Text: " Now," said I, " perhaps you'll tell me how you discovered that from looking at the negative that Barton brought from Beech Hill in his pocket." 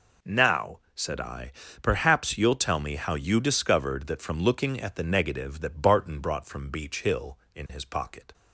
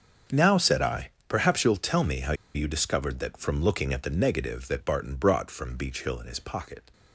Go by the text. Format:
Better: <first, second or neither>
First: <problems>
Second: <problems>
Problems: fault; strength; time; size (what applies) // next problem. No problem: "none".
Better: first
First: none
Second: starts louder than the rest; until 1.3 s; 6 dB // pauses between "how" and "you"; slight; at 2.3 s; 0.21 s long